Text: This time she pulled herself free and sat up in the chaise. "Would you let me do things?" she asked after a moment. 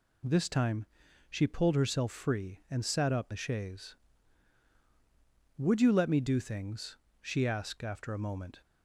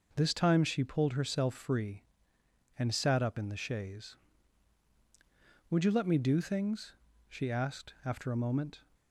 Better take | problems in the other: second | pauses between "time" and "she"; at 0.8 s; 0.44 s long // skips "in"; at 3.3 s

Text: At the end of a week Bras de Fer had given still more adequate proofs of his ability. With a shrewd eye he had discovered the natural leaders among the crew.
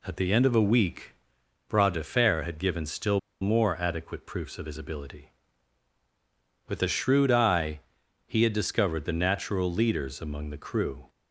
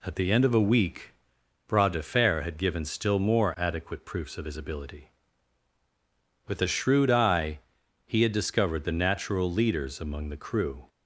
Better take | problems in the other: second | pauses between "week" and "Bras"; noticeable; at 1.1 s; 0.54 s long; noticeable in the second // pauses between "still" and "more"; slight; at 3.1 s; 0.21 s long // pauses between "eye" and "he"; at 7.8 s; 0.44 s long; also in the second

